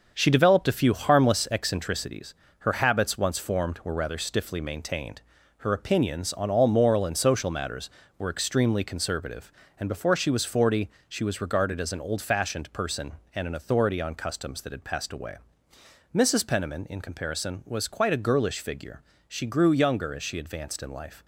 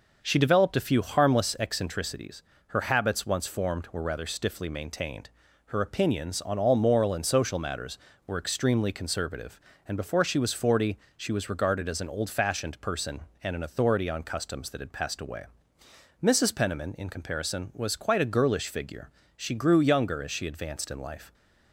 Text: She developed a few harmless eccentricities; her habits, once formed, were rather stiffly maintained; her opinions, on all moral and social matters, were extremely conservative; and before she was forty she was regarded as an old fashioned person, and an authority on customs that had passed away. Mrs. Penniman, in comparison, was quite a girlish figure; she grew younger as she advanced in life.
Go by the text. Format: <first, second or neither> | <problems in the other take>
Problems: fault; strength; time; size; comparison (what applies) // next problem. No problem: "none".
second | gets quieter; throughout; 6.5 dB // pauses between "forty" and "she"; slight; at 10.8 s; 0.20 s long; slight in the second